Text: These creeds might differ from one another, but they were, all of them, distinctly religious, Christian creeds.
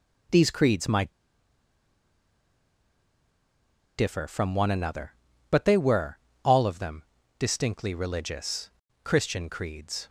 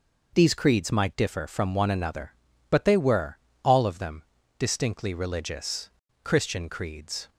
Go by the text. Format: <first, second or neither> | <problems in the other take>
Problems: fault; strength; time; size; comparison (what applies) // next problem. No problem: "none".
second | pauses between "might" and "differ"; strong; at 1.1 s; 2.8 s long